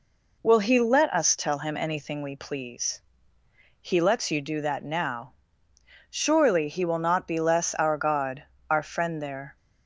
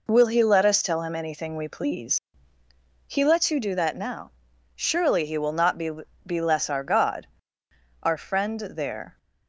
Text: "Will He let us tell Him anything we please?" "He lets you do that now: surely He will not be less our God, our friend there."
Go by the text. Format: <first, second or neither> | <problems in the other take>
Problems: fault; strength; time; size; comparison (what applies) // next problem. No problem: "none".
first | says "be" twice; at 6.2 s